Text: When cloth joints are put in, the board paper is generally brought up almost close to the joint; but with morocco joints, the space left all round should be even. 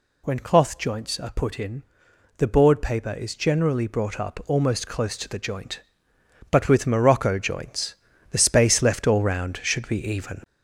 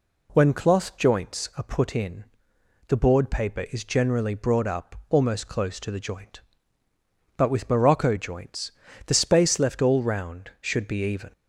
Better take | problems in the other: second | gets louder; noticeable; throughout; 5 dB

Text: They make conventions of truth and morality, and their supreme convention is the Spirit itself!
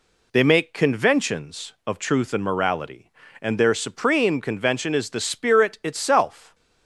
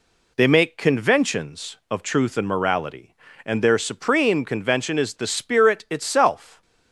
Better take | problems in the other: neither | none

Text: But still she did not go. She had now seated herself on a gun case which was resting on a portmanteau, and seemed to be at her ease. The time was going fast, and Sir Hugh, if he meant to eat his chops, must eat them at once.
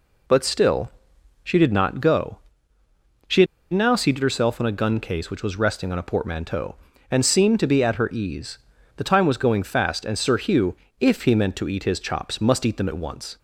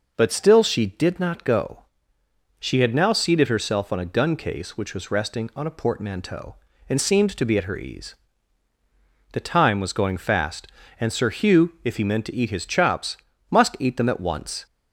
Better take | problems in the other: second | pauses between "still" and "she"; noticeable; at 0.8 s; 0.54 s long // pauses between "had" and "now"; slight; at 3.4 s; 0.27 s long

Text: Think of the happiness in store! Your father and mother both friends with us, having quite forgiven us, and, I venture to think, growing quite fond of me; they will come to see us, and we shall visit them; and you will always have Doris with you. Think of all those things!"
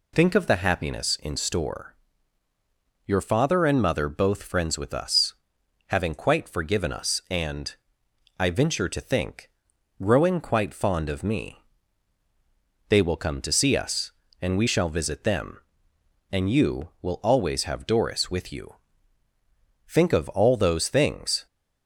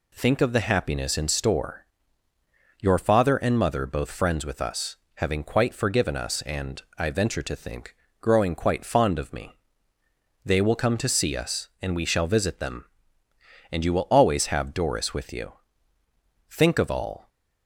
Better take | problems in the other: first | stops before "those things"; at 17.2 s

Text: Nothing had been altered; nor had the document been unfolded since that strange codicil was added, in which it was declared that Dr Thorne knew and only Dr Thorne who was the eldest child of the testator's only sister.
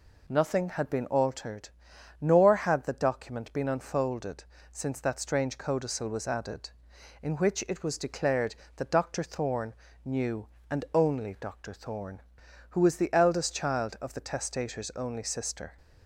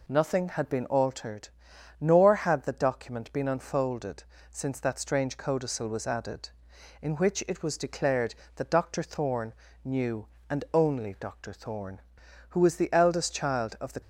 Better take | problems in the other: first | pauses between "unfolded" and "since"; slight; at 4.2 s; 0.28 s long; slight in the first // pauses between "Thorne" and "knew"; slight; at 9.5 s; 0.32 s long; slight in the first // stops before "testator's only sister"; at 14.0 s

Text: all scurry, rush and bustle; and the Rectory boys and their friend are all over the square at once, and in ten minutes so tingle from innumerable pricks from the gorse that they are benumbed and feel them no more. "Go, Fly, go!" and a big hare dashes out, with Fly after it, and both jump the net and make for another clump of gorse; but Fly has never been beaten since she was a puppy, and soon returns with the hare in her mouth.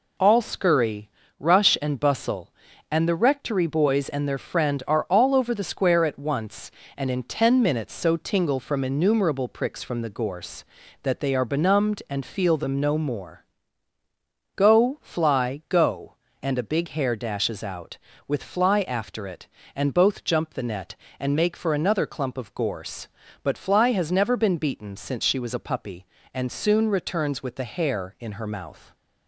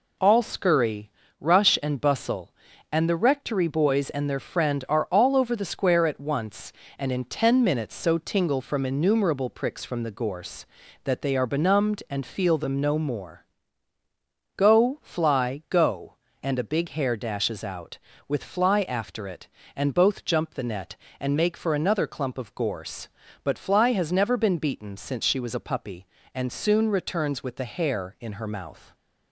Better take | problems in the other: neither | none

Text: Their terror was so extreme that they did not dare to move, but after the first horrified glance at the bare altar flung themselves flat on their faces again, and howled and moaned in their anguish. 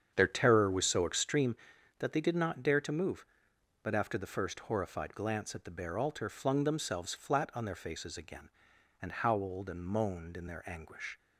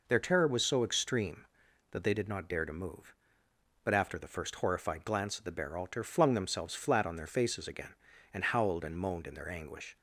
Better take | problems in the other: second | starts louder than the rest; strong; until 1.5 s; 8 dB

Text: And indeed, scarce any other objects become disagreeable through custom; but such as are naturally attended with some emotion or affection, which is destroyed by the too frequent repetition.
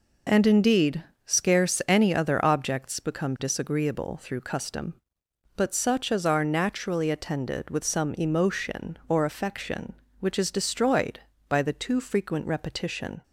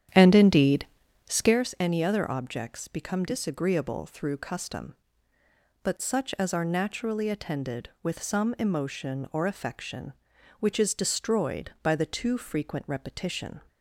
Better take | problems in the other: first | starts louder than the rest; strong; until 1.6 s; 9.5 dB

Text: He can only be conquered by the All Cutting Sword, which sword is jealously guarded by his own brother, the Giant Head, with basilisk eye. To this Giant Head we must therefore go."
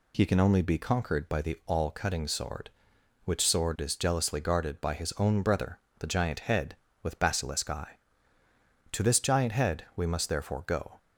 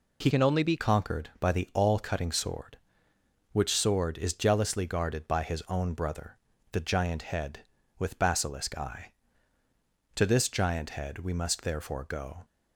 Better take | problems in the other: first | changes voice from "can" to "be"; from 0.2 to 0.7 s; 0.5 s long

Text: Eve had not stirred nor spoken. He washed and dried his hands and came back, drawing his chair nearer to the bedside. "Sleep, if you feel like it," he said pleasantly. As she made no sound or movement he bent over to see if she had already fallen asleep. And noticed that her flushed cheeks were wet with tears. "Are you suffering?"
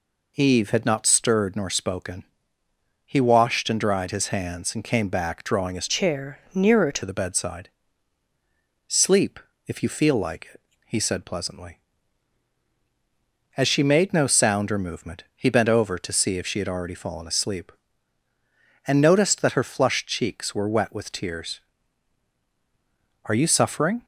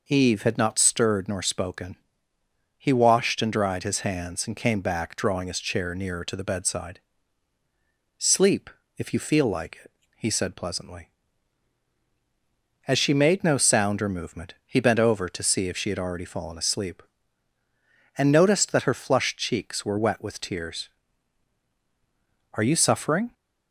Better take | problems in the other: second | changes voice from "chair" to "to"; from 5.8 to 7.0 s; 1.2 s long

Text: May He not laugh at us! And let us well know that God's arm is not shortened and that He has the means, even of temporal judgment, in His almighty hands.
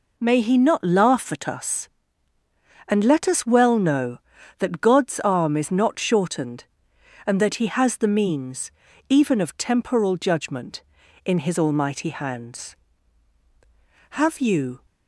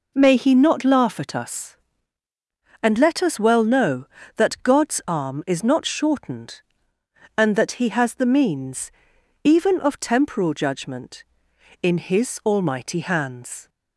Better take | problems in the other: second | goes on to say "Have you"; noticeable; from 14.1 s on; 0.74 s long

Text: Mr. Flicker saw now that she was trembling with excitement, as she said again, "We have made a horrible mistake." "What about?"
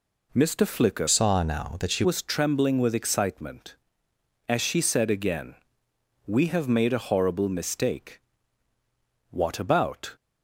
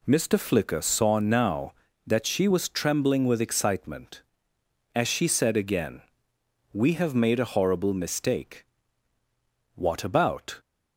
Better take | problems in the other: second | changes voice from "saw" to "she"; from 1.0 to 2.0 s; 1.0 s long

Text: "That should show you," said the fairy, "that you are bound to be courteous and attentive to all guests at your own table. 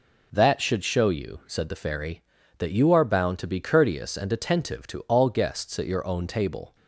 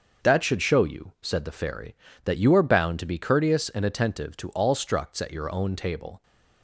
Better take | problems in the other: first | starts louder than the rest; until 1.2 s; 6.5 dB // says "structs" for "guests"; at 4.7 s

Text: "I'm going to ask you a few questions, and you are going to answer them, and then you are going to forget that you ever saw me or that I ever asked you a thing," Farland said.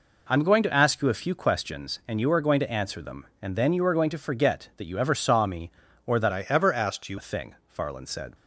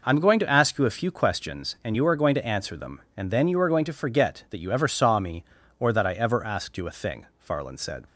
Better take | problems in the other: second | changes voice from "I" to "you"; from 6.3 to 7.1 s; 0.8 s long

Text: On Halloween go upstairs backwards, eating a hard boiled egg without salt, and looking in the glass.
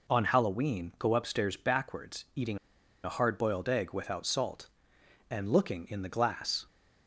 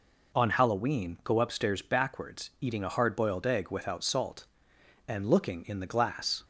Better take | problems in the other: second | pauses between "eating" and "a"; noticeable; at 2.5 s; 0.46 s long

